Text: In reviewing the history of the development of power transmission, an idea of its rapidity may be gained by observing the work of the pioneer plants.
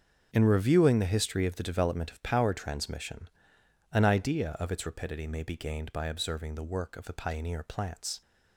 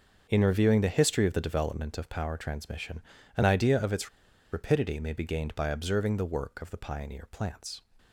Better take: first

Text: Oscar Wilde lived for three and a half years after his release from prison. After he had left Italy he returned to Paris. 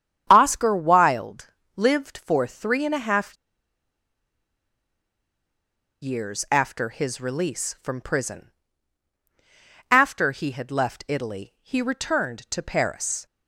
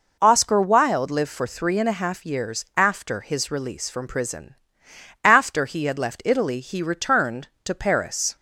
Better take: second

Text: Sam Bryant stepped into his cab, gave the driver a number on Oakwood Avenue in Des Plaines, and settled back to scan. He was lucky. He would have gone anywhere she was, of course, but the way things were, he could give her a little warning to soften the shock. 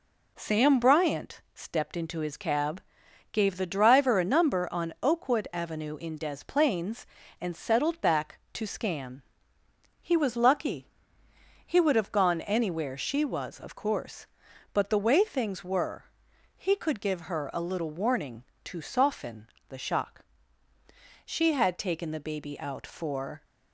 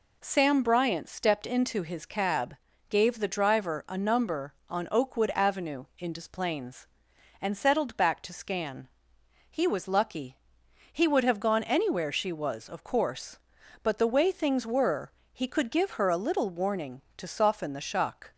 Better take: second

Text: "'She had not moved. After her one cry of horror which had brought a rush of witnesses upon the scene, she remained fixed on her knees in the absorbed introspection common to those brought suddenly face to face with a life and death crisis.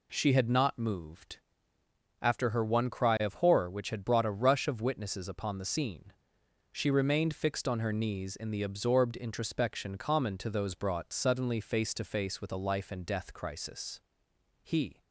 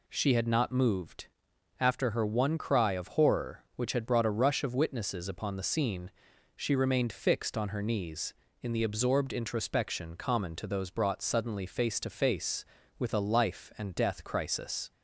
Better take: second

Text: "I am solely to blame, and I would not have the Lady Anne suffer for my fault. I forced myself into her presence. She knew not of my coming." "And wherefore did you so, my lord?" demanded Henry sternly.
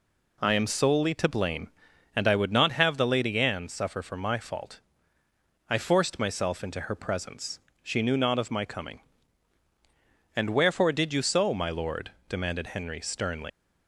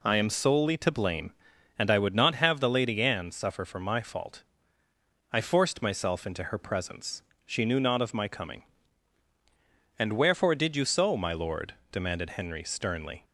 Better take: second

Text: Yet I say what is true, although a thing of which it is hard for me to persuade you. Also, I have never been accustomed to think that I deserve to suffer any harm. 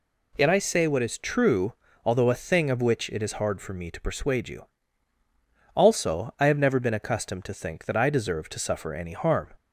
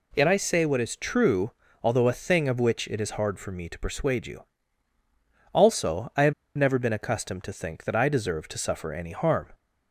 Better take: first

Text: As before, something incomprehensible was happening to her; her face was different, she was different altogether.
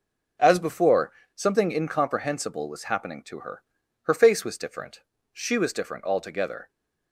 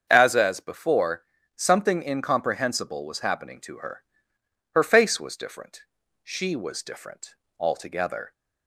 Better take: first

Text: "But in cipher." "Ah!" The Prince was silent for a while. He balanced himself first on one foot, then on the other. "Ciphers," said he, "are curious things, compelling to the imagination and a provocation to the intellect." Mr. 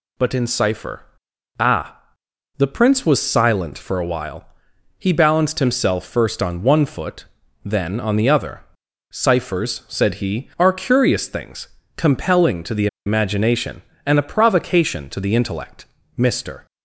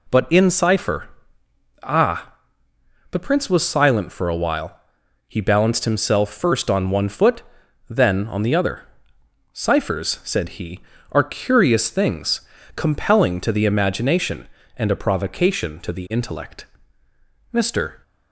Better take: second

